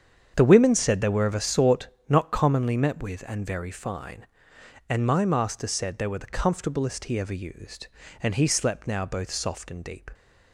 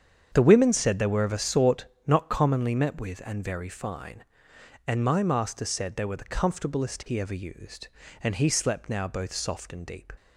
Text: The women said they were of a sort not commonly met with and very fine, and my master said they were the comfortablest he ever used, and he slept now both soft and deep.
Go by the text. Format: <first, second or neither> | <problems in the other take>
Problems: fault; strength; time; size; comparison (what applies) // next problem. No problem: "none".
neither | starts louder than the rest; strong; the same in both // pauses between "sort" and "not"; slight; the same in both